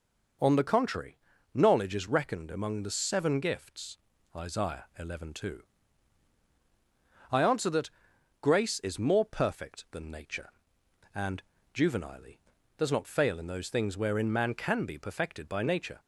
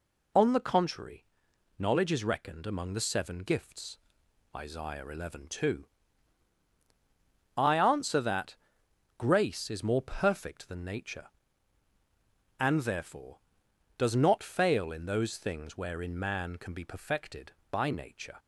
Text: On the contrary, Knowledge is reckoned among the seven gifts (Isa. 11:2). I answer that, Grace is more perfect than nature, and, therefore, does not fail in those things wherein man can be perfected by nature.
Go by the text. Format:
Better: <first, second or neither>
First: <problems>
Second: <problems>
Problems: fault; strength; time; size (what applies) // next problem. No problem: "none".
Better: second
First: says "juvenilely" for "therefore"; at 11.7 s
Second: none